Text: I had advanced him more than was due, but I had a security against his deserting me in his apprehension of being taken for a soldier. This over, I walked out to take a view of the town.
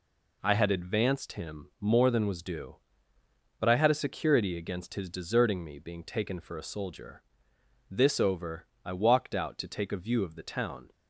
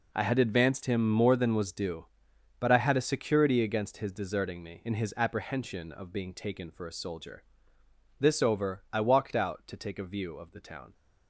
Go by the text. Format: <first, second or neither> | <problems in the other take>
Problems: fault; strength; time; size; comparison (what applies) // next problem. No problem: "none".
second | skips "in his apprehension of"; at 5.7 s